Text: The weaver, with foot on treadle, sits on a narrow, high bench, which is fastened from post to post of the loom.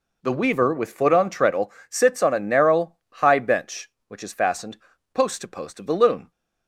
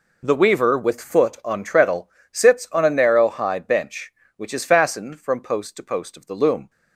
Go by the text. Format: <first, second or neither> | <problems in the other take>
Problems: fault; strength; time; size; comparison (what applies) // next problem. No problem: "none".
second | skips "from"; at 4.9 s